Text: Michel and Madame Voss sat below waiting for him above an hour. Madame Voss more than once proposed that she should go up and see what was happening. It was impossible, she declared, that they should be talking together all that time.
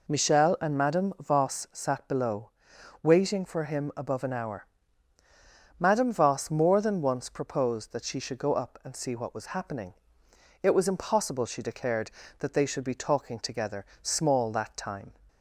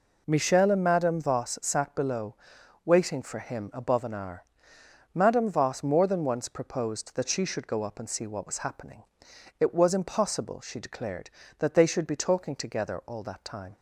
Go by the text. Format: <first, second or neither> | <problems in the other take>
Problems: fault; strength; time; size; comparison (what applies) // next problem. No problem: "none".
second | pauses between "below" and "waiting"; noticeable; at 2.5 s; 0.52 s long; noticeable in the second // says "small" for "all"; at 14.0 s